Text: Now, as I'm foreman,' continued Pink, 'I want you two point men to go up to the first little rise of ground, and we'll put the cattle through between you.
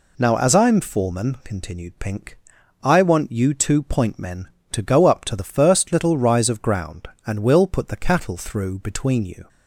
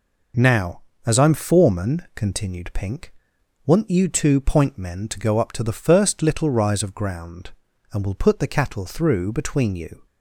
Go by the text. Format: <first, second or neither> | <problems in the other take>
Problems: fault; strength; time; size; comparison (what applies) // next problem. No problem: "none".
first | skips "I"; at 3.3 s